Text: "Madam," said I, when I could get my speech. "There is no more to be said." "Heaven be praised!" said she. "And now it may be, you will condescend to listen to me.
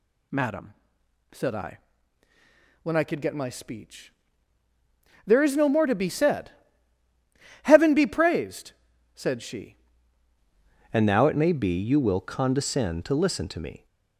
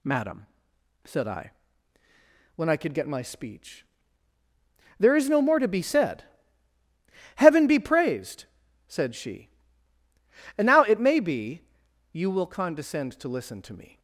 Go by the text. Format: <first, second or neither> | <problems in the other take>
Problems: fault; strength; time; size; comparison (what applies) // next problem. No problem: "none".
second | changes voice at "And"; from 10.9 s on; 2.9 s long